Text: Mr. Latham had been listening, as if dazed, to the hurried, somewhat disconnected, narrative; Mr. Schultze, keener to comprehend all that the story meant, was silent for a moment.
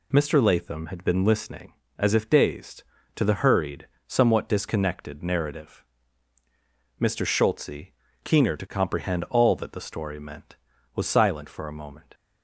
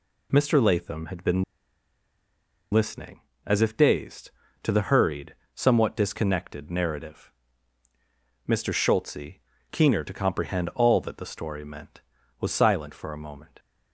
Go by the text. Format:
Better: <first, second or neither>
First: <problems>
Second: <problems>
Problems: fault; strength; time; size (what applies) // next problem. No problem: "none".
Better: first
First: none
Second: pauses between "been" and "listening"; strong; at 1.4 s; 1.2 s long